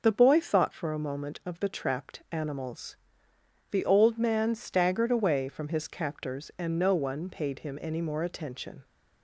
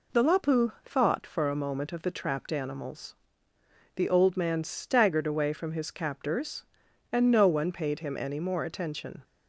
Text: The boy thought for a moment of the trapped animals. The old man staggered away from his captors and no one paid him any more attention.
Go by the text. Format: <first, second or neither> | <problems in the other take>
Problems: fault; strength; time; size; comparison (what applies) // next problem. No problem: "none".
first | says "lapu" for "boy"; at 0.2 s